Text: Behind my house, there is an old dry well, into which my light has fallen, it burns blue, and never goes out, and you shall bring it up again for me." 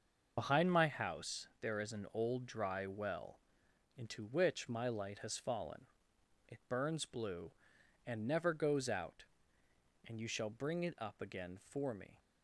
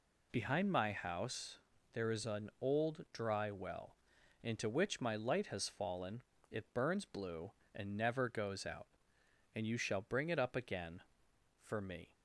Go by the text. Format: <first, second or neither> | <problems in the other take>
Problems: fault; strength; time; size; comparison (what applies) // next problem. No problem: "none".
second | loses the start of "Behind"; at 0.3 s; 30 ms // starts louder than the rest; until 1.3 s; 6 dB